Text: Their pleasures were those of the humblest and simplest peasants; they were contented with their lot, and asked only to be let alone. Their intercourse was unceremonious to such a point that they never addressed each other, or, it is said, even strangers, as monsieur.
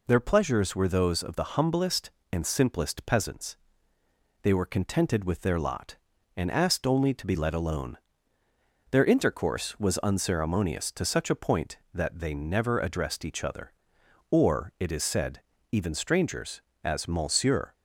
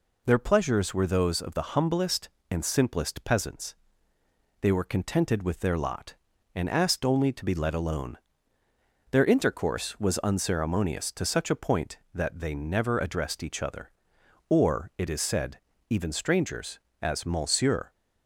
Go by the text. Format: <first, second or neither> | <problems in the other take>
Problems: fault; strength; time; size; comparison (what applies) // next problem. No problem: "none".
neither | none